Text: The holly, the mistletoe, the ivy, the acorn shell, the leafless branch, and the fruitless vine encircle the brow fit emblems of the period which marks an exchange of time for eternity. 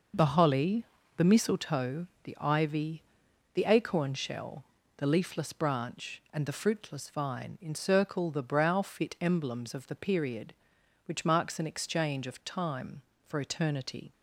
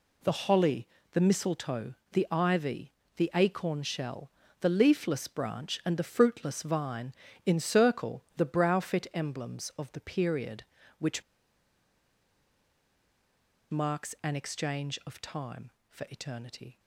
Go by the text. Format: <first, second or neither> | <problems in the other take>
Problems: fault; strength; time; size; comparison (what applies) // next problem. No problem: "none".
first | pauses between "vine" and "encircle"; slight; at 7.1 s; 0.34 s long // pauses between "which" and "marks"; strong; at 11.2 s; 2.4 s long